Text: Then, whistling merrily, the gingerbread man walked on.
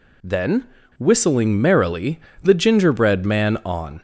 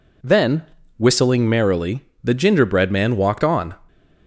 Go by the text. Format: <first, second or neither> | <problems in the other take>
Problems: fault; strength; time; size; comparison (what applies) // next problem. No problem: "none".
second | skips "walked"; at 3.6 s